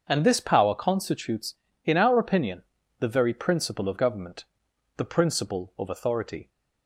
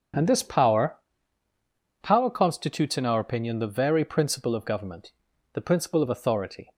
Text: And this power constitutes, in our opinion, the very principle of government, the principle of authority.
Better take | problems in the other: first | starts louder than the rest; strong; until 2.2 s; 7.5 dB; also in the first // says "power" twice; at 2.0 s

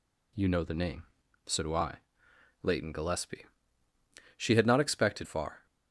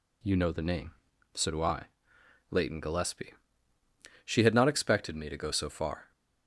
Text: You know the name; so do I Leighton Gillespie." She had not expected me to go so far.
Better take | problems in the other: second | pauses between "I" and "Leighton"; noticeable; at 1.9 s; 0.66 s long; noticeable in the second // skips "me to go so"; at 5.2 s

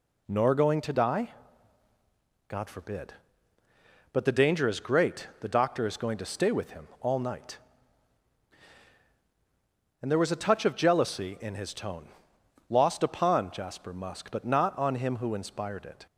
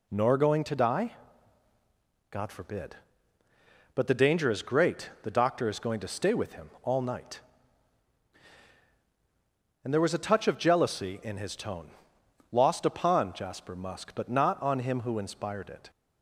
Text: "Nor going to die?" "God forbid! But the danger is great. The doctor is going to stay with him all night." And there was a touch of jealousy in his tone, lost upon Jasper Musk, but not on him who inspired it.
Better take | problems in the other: neither | none

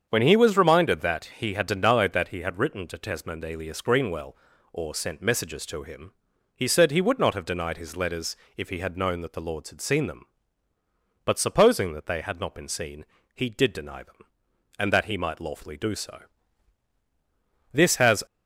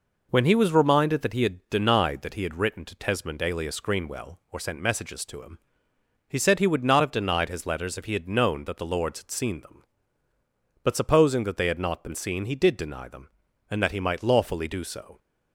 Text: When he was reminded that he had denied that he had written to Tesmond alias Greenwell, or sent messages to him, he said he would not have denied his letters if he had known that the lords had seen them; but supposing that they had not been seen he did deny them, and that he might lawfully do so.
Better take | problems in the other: second | starts louder than the rest; strong; until 1.1 s; 7.5 dB // pauses between "letters" and "if"; slight; at 8.3 s; 0.20 s long // pauses between "seen" and "he"; slight; at 13.0 s; 0.32 s long // goes on to say "This has"; from 17.7 s on; 0.50 s long

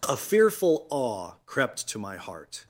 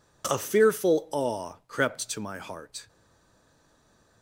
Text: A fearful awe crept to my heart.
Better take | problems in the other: first | stays silent after the last word; noticeable; from 2.8 s on; 1.4 s long

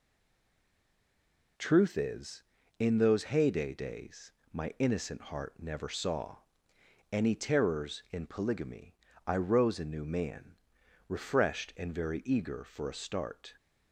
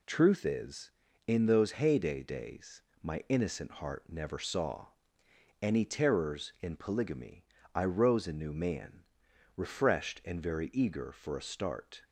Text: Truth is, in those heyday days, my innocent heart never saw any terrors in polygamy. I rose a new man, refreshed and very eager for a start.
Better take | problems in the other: second | stays silent before the first word; noticeable; until 1.5 s; 1.5 s long // pauses between "saw" and "any"; noticeable; at 6.3 s; 0.74 s long; noticeable in the second

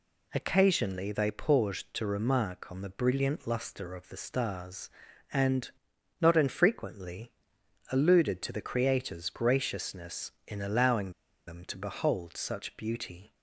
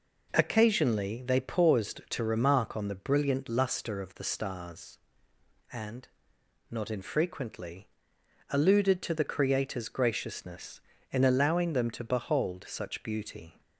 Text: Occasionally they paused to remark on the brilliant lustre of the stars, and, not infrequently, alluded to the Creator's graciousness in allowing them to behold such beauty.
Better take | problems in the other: second | pauses between "allowing" and "them"; at 11.0 s; 0.37 s long

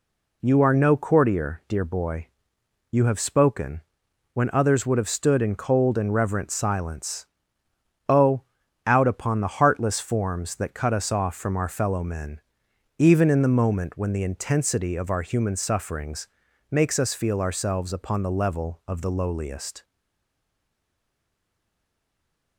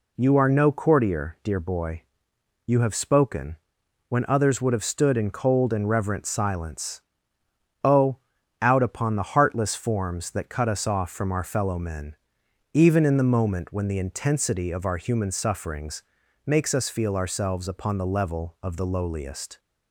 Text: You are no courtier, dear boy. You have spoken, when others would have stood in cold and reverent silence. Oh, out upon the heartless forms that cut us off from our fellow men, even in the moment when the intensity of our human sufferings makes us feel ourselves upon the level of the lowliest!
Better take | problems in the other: second | pauses between "sufferings" and "makes"; at 16.2 s; 0.44 s long; also in the second // stays silent after the last word; strong; from 19.8 s on; 2.7 s long

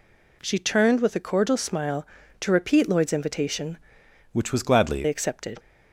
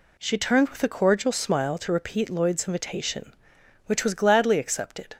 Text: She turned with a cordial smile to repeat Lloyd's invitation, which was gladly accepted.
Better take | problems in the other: second | changes voice from "which" to "gladly"; from 4.3 to 5.0 s; 0.7 s long

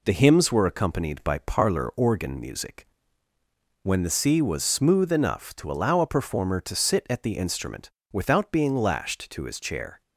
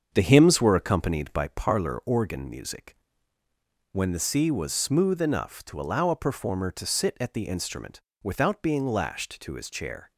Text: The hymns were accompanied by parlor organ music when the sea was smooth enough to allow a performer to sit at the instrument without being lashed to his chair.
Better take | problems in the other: first | starts louder than the rest; strong; until 1.5 s; 7 dB // pauses between "music" and "when"; noticeable; at 2.9 s; 0.96 s long; noticeable in the first // pauses between "instrument" and "without"; slight; at 8.0 s; 0.20 s long; slight in the first

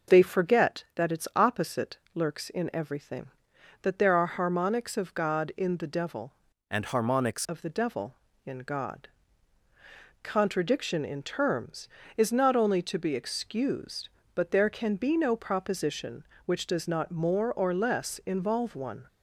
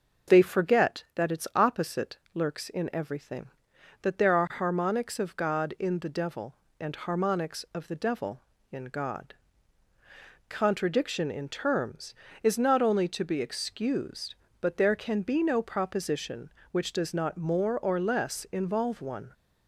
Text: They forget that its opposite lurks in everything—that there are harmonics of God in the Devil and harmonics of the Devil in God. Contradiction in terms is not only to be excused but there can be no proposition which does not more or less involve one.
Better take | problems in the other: second | pauses between "opposite" and "lurks"; slight; at 1.9 s; 0.16 s long; slight in the second // changes voice from "and" to "harmonics"; from 6.6 to 7.4 s; 0.8 s long

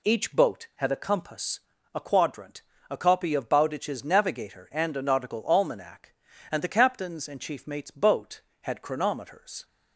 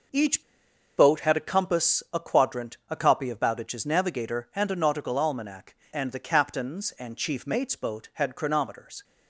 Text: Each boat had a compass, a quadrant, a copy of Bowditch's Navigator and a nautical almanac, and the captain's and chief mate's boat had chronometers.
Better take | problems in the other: first | pauses between "Each" and "boat"; noticeable; at 0.4 s; 0.56 s long

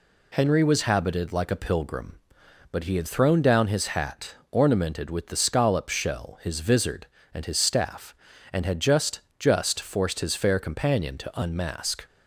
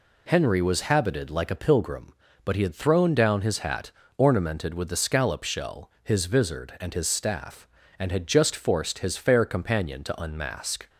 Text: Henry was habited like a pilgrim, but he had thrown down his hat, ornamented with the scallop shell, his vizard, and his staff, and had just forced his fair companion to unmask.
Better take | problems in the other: second | says "just" twice; at 9.3 s

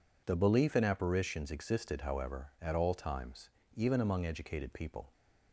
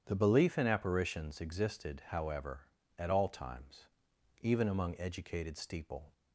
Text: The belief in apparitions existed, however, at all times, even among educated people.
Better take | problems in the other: first | starts louder than the rest; strong; until 1.0 s; 9 dB // says "steeple" for "people"; at 5.5 s

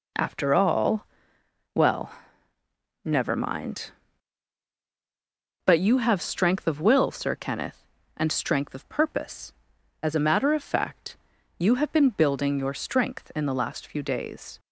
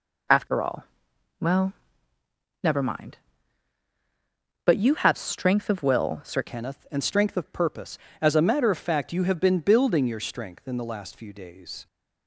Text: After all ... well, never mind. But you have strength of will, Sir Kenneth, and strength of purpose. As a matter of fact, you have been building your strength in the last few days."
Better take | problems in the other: first | changes voice at "Kenneth"; from 6.4 s on; 5.4 s long

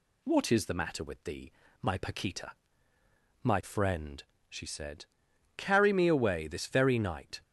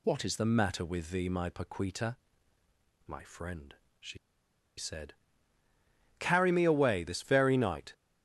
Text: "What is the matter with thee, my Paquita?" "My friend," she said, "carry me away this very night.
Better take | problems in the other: first | pauses between "she" and "said"; noticeable; at 4.1 s; 0.61 s long

